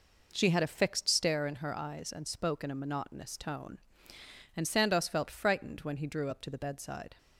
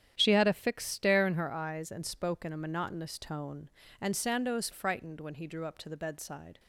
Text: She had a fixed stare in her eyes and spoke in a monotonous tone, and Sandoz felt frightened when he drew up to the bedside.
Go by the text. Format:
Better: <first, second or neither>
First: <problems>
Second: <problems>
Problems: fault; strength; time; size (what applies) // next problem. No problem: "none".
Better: first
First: none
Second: starts louder than the rest; strong; until 1.1 s; 10 dB // skips "felt"; at 4.7 s